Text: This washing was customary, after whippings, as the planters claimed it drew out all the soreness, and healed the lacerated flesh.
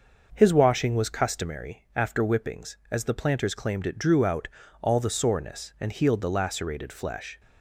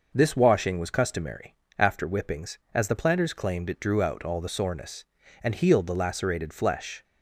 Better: second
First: starts louder than the rest; noticeable; until 1.3 s; 6 dB // says "His" for "This"; at 0.3 s // pauses between "out" and "all"; slight; at 4.4 s; 0.34 s long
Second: none

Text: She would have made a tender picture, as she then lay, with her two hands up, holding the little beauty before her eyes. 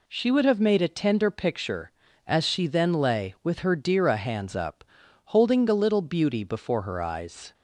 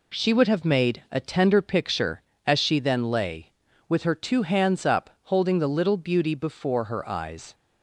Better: second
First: says "dira" for "two"; at 3.7 s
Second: none

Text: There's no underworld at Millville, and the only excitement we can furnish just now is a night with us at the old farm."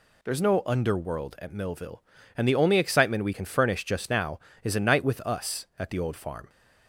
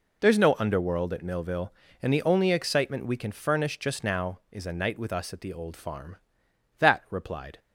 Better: first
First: none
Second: goes on to say "That replied"; noticeable; from 6.7 s on; 0.80 s long

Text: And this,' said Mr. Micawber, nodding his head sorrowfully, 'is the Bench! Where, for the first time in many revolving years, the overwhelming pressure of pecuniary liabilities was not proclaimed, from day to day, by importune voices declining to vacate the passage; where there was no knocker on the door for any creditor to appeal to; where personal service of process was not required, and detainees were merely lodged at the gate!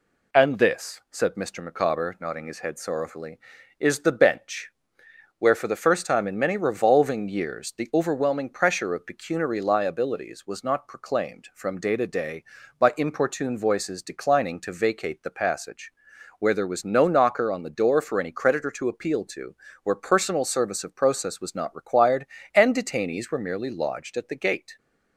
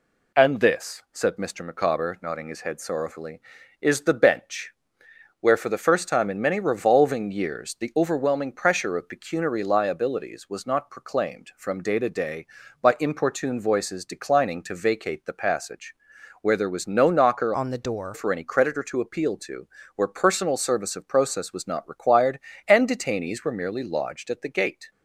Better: first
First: none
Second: changes voice from "on" to "door"; from 17.5 to 18.1 s; 0.6 s long

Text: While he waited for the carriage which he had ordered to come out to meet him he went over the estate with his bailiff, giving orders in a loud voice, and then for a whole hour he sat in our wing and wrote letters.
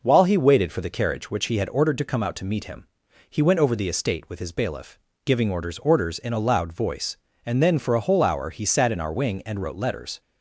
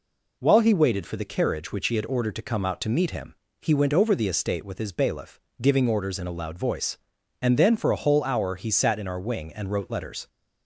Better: second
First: pauses between "him" and "he"; at 2.8 s; 0.42 s long // says "orders" twice; at 5.8 s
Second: pauses between "him" and "he"; slight; at 3.3 s; 0.28 s long

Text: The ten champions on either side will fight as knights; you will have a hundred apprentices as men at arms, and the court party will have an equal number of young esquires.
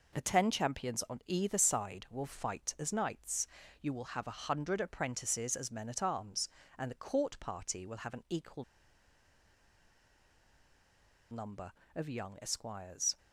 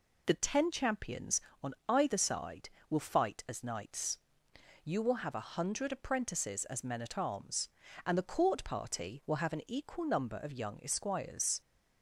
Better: second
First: pauses between "equal" and "number"; strong; at 8.6 s; 2.6 s long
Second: none

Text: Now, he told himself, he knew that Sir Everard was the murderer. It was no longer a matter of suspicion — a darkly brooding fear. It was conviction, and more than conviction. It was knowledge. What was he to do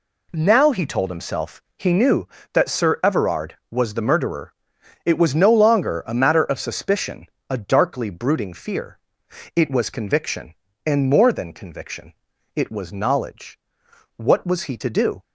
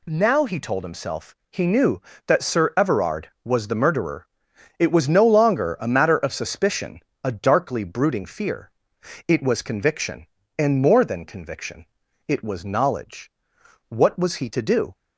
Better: second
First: starts louder than the rest; slight; until 2.1 s; 2 dB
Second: none

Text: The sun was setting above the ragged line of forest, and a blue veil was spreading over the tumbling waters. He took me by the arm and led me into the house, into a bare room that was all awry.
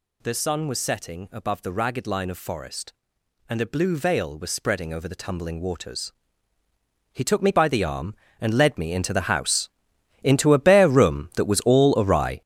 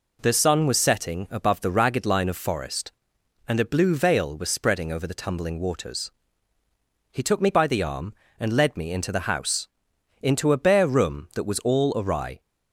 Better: second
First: gets louder; strong; throughout; 10 dB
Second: none

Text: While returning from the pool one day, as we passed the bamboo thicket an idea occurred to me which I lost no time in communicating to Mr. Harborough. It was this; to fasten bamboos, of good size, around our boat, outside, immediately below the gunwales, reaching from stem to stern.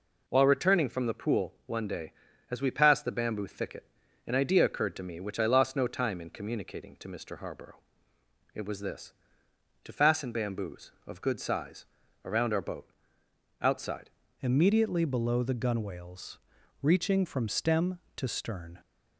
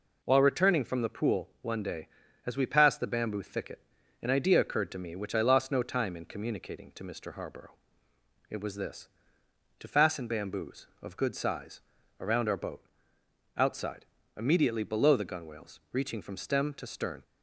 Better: second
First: pauses between "thicket" and "an"; at 3.8 s; 0.44 s long // changes voice at "immediately"; from 14.4 s on; 4.3 s long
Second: pauses between "thicket" and "an"; at 3.7 s; 0.44 s long

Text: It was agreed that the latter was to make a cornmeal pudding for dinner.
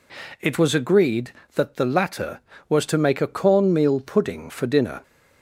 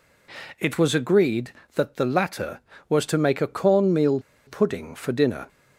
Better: first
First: none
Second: pauses between "cornmeal" and "pudding"; slight; at 4.1 s; 0.27 s long

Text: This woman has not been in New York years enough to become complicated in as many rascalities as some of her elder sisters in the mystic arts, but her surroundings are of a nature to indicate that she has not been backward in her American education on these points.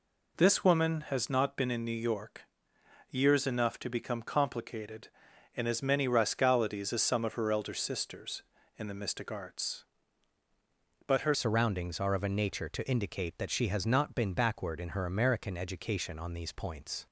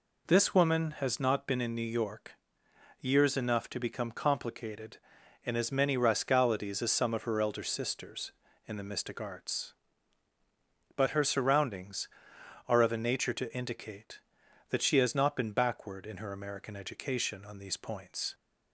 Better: second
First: pauses between "York" and "years"; noticeable; at 2.4 s; 0.68 s long // changes voice at "surroundings"; from 11.3 s on; 5.7 s long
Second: pauses between "York" and "years"; noticeable; at 2.3 s; 0.68 s long

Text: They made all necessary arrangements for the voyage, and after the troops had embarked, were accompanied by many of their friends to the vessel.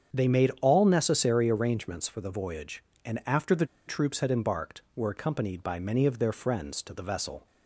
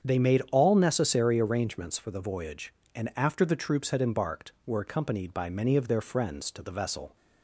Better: second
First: starts louder than the rest; strong; until 1.2 s; 7.5 dB // pauses between "the" and "troops"; slight; at 3.6 s; 0.22 s long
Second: starts louder than the rest; strong; until 1.1 s; 7.5 dB

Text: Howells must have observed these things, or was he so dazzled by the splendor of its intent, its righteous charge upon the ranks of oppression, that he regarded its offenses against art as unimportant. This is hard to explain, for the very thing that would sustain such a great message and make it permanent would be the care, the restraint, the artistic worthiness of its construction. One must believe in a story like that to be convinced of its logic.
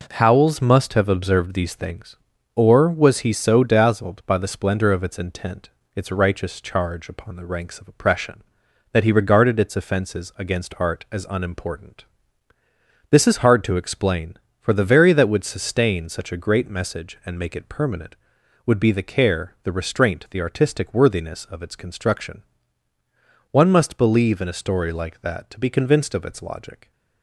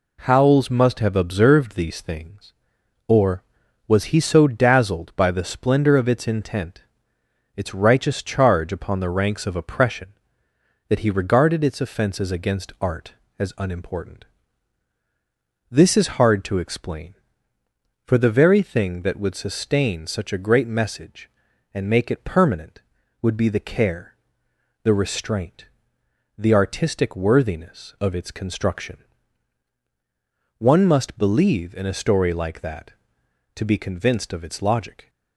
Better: second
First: skips "thing"; at 15.1 s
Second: none

